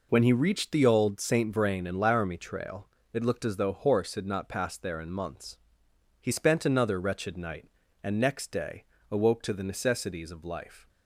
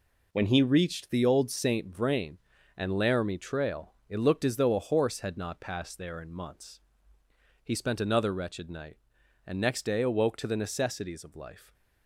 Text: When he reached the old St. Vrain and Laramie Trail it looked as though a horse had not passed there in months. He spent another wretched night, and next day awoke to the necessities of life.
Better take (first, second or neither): second